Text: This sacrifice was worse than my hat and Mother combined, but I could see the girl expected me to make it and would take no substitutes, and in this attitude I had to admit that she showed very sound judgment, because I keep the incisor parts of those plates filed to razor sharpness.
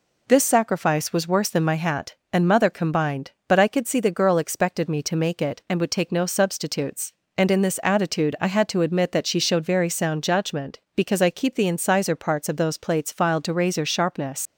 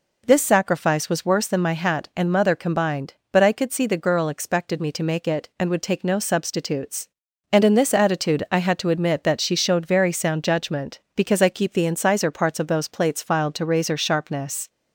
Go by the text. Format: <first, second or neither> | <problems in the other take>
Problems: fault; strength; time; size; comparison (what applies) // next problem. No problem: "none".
second | leaves "sharpness" unfinished; at 14.4 s; 95 ms